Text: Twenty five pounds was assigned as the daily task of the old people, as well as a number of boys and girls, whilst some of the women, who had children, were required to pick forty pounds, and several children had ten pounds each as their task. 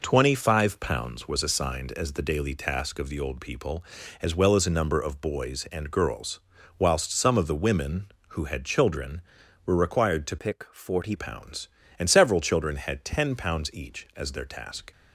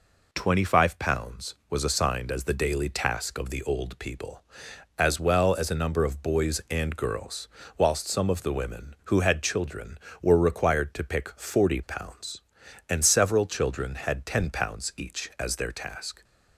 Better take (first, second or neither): second